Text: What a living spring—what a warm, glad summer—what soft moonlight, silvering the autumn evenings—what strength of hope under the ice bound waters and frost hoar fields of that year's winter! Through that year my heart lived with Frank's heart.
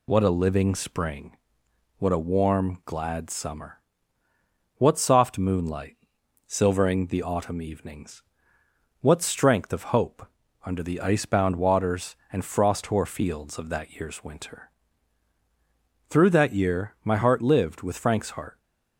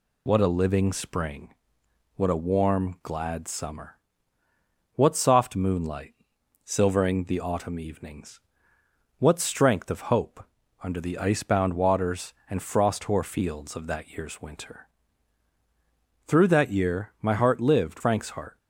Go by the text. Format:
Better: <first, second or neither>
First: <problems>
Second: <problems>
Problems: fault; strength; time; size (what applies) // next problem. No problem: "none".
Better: first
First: pauses between "hope" and "under"; at 10.2 s; 0.40 s long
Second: pauses between "hope" and "under"; at 10.4 s; 0.40 s long // skips "with"; at 18.0 s